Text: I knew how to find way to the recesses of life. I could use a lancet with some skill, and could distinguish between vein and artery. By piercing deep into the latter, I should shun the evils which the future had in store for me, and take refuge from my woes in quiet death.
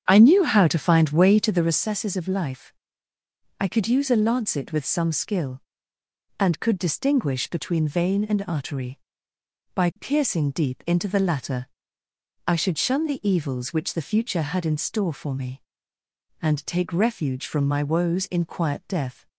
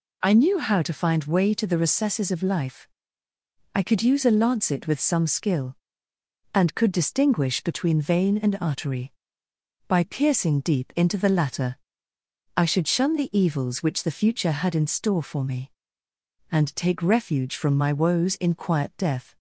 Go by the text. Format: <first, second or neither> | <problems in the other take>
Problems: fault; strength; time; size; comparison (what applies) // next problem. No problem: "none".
second | starts louder than the rest; strong; until 1.8 s; 8.5 dB